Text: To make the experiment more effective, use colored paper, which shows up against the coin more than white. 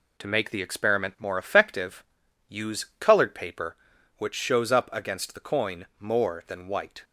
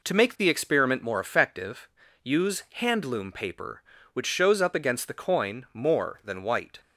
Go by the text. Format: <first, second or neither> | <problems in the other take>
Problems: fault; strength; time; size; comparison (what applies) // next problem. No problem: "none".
first | says "handloom" for "colored"; at 2.7 s